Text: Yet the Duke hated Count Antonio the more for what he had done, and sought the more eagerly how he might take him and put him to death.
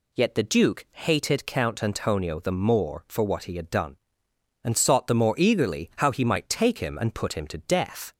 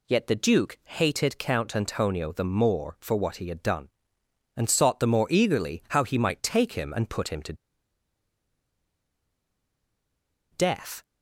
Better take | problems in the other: first | pauses between "to" and "death"; strong; at 7.5 s; 2.9 s long

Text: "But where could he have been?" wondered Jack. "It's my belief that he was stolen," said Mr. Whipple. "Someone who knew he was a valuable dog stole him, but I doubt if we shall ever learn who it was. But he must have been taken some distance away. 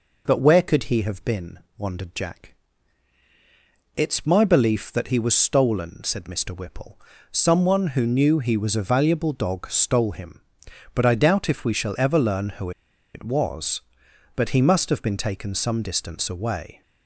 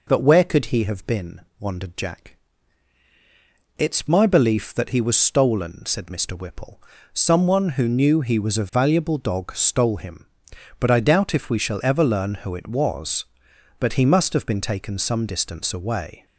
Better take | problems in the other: second | pauses between "who" and "it"; noticeable; at 12.6 s; 0.46 s long

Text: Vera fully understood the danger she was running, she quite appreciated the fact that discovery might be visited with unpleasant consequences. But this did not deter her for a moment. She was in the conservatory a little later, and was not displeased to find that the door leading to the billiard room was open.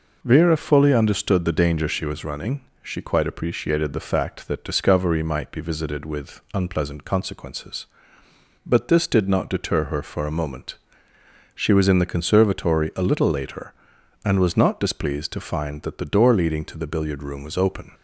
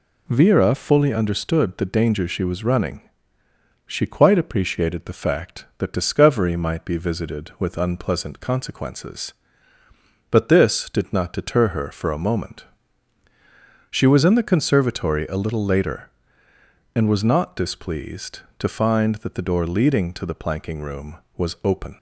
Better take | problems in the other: first | says "planking" for "billiard"; at 20.3 s

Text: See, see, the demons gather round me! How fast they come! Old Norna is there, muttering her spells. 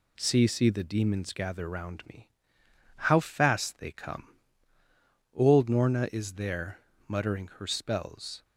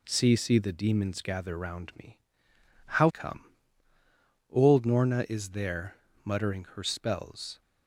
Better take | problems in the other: first | skips "fast they"; at 3.0 s

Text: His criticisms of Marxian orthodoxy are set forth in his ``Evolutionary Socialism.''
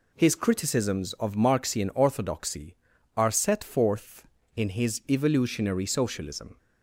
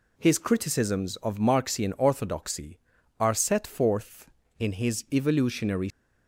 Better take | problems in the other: first | stops before "Socialism"; at 5.8 s

